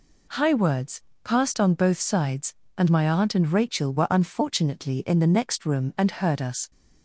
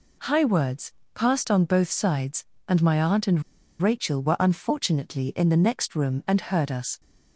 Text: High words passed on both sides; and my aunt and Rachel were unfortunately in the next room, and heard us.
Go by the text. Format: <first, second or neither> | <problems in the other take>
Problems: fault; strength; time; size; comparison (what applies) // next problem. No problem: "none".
first | pauses between "words" and "passed"; slight; at 0.9 s; 0.22 s long; slight in the first // pauses between "and" and "Rachel"; at 3.4 s; 0.39 s long